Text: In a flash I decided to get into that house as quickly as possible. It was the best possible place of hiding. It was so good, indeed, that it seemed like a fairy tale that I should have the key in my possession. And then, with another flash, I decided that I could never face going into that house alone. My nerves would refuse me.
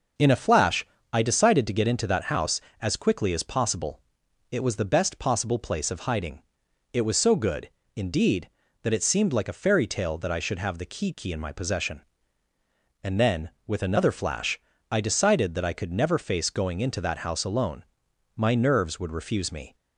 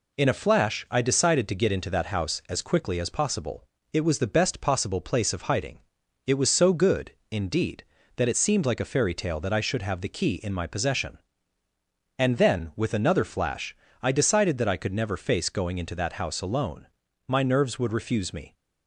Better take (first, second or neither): second